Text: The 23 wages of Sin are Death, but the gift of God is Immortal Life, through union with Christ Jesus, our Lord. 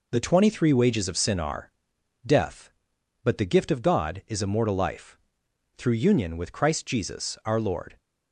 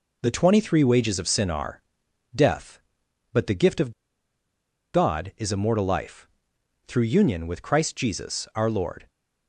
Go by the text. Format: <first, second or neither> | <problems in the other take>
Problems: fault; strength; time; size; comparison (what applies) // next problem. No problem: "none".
first | pauses between "are" and "Death"; noticeable; at 1.7 s; 0.54 s long; noticeable in the first // pauses between "of" and "God"; at 3.9 s; 1.0 s long